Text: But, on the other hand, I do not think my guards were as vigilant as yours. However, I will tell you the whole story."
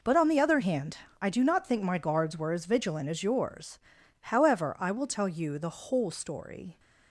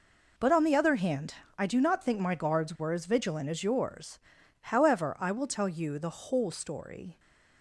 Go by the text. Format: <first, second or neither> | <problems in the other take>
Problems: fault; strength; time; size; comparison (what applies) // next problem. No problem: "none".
neither | none